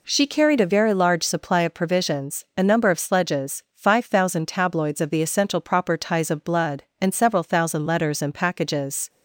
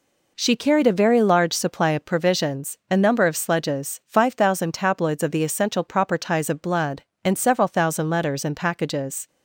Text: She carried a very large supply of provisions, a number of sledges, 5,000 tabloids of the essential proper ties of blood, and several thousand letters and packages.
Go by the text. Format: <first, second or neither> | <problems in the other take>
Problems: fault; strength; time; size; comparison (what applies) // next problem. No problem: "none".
neither | none